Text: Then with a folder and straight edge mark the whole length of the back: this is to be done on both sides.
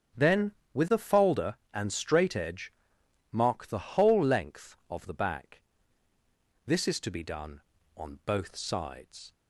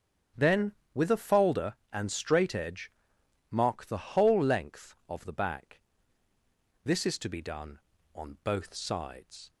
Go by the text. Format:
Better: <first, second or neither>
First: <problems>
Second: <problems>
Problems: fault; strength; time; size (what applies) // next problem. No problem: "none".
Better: neither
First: starts louder than the rest; strong; until 1.4 s; 8 dB // pauses between "edge" and "mark"; noticeable; at 2.7 s; 0.60 s long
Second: starts louder than the rest; strong; until 1.5 s; 8.5 dB // pauses between "edge" and "mark"; noticeable; at 2.9 s; 0.60 s long